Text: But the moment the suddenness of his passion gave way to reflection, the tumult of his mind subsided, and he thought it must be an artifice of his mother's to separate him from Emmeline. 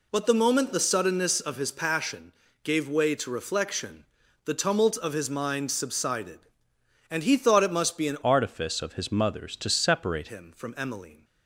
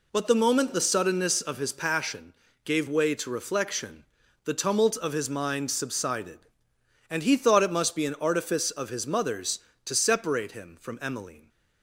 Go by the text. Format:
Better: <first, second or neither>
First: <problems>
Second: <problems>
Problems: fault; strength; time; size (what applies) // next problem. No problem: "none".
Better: second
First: pauses between "passion" and "gave"; slight; at 2.3 s; 0.32 s long // changes voice from "artifice" to "separate"; from 8.2 to 10.2 s; 2.0 s long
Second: pauses between "passion" and "gave"; slight; at 2.3 s; 0.32 s long